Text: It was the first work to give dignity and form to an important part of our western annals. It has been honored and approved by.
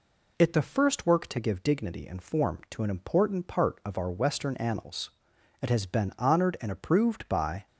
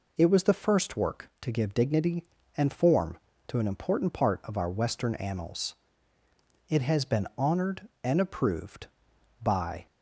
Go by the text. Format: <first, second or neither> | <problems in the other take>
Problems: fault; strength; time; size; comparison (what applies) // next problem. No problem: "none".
second | skips "was"; at 0.5 s